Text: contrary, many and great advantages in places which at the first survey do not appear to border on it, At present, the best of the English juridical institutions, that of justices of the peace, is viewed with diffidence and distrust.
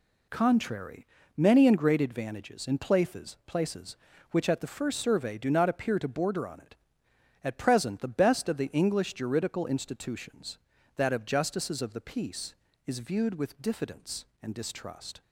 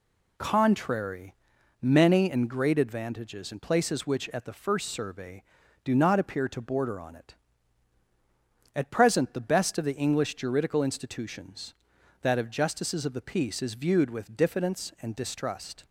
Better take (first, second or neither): second